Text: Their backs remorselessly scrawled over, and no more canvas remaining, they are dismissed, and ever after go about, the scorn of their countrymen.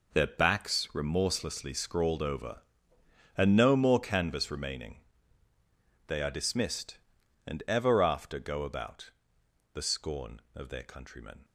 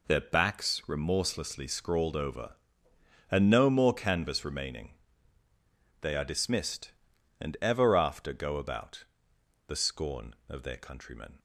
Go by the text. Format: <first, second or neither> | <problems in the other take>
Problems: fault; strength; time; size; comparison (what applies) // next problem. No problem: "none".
second | gets quieter; strong; throughout; 12.5 dB